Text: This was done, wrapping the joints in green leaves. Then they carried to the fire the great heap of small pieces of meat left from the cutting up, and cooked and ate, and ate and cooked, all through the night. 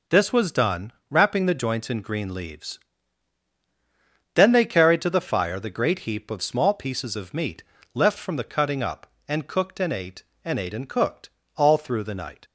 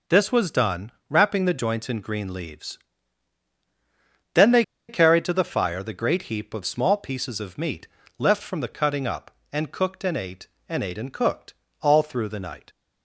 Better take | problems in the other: first | pauses between "they" and "carried"; slight; at 4.6 s; 0.26 s long // pauses between "meat" and "left"; slight; at 7.8 s; 0.28 s long; slight in the first

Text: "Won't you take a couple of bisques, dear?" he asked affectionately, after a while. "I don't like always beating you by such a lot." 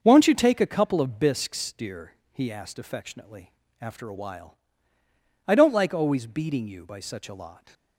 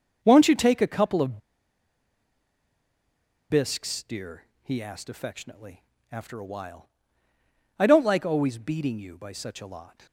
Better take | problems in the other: first | starts louder than the rest; until 1.2 s; 6.5 dB; also in the first // pauses between "of" and "bisques"; strong; at 1.3 s; 2.1 s long

